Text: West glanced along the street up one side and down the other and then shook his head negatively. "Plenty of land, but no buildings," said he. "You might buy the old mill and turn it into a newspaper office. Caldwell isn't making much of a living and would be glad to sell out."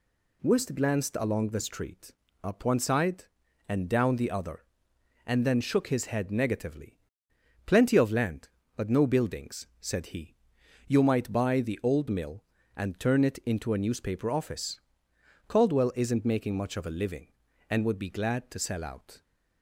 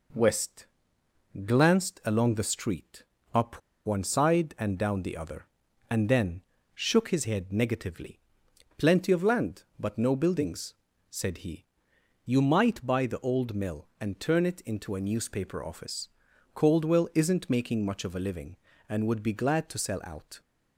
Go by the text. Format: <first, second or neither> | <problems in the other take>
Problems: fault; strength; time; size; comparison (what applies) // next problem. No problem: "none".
first | pauses between "West" and "glanced"; noticeable; at 0.6 s; 0.80 s long // pauses between "street" and "up"; slight; at 3.0 s; 0.30 s long; slight in the first // pauses between "up" and "one"; slight; at 3.6 s; 0.26 s long // pauses between "then" and "shook"; slight; at 6.4 s; 0.32 s long